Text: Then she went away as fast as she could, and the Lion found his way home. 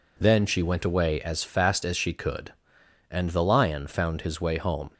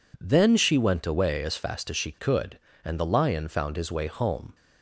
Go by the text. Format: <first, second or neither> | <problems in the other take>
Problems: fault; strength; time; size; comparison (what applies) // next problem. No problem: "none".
neither | none